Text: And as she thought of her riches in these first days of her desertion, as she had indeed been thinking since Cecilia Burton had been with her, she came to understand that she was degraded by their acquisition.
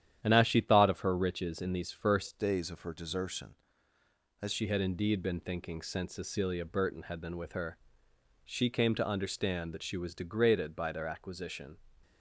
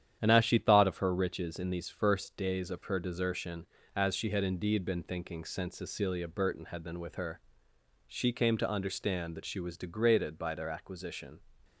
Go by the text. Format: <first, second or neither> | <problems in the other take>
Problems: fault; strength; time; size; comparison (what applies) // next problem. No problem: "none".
second | starts louder than the rest; strong; until 1.2 s; 10.5 dB; strong in the second // changes voice from "days" to "as"; from 2.3 to 4.5 s; 2.2 s long